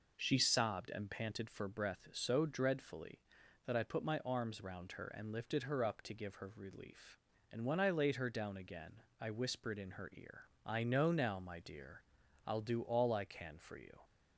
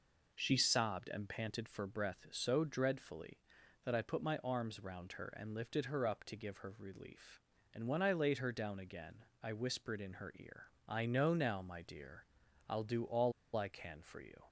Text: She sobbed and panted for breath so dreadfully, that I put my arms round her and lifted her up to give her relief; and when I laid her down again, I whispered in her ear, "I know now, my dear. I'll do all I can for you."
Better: first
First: none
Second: pauses between "all" and "I"; slight; at 13.3 s; 0.24 s long

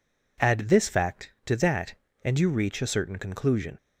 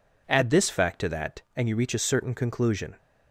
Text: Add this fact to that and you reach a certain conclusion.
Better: neither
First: none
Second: none

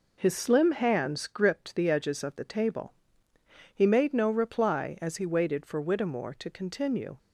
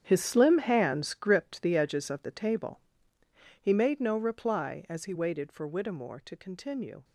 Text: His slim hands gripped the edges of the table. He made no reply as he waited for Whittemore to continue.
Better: first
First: none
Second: gets quieter; strong; throughout; 12 dB

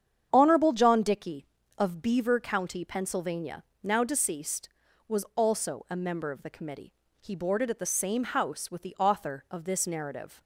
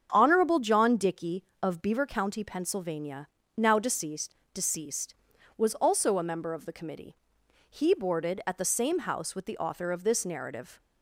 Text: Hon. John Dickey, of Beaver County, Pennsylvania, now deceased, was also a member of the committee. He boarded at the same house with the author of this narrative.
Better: first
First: starts louder than the rest; strong; until 1.3 s; 8.5 dB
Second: starts louder than the rest; strong; until 1.1 s; 7.5 dB // says "deceased" twice; at 4.5 s

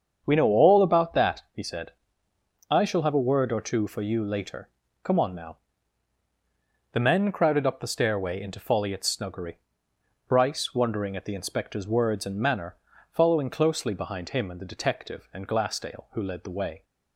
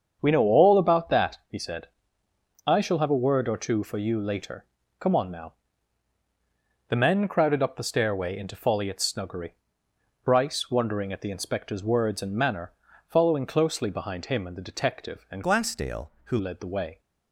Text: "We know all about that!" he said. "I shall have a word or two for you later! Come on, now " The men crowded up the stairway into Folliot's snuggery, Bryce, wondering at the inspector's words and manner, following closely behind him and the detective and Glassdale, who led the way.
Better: first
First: starts louder than the rest; strong; until 1.2 s; 7.5 dB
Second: starts louder than the rest; strong; until 1.2 s; 7.5 dB // changes voice from "Glassdale" to "who"; from 15.4 to 16.3 s; 0.9 s long

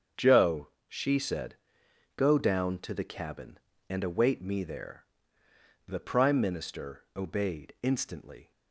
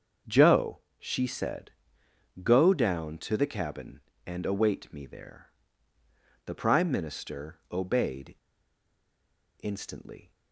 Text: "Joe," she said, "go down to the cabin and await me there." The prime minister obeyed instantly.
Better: first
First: starts louder than the rest; strong; until 1.3 s; 7 dB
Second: starts louder than the rest; until 1.4 s; 6.5 dB // pauses between "obeyed" and "instantly"; strong; at 8.3 s; 1.2 s long

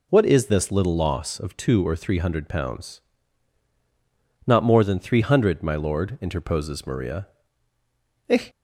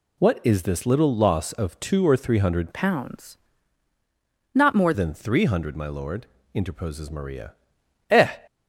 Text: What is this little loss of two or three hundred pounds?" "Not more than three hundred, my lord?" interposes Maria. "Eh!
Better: first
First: none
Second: changes voice from "pounds" to "more"; from 2.7 to 4.9 s; 2.2 s long

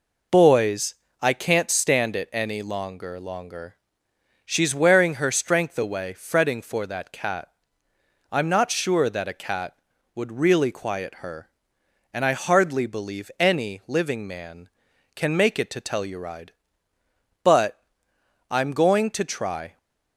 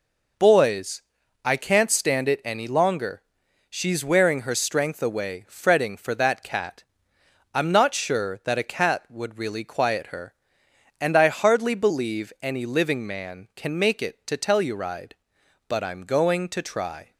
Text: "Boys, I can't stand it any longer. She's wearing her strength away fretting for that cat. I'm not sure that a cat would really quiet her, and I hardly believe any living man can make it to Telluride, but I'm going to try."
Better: second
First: says "longer" twice; at 3.1 s // pauses between "but" and "I'm"; noticeable; at 17.8 s; 0.70 s long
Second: none

